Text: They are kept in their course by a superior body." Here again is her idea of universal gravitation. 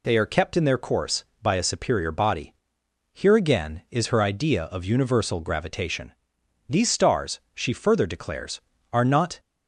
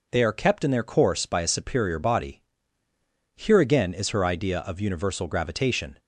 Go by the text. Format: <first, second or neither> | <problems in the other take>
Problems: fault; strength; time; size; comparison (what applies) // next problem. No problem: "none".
second | goes on to say "These stars she further declares are not"; strong; from 6.6 s on; 2.7 s long